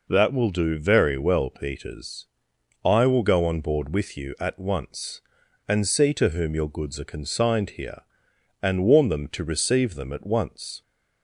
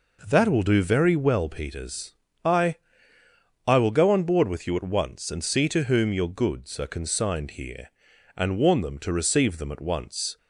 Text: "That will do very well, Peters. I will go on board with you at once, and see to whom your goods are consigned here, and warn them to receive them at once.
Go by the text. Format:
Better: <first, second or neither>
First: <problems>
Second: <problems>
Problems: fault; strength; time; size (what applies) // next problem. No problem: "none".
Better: first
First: none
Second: says "I" twice; at 3.6 s